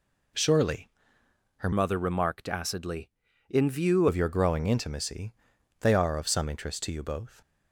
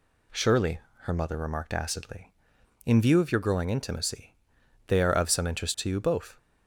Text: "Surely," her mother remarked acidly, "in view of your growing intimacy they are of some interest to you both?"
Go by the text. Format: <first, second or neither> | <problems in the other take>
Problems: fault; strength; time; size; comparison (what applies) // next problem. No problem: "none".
second | changes voice from "mother" to "view"; from 1.7 to 4.0 s; 2.3 s long // pauses between "intimacy" and "they"; noticeable; at 5.3 s; 0.46 s long; noticeable in the second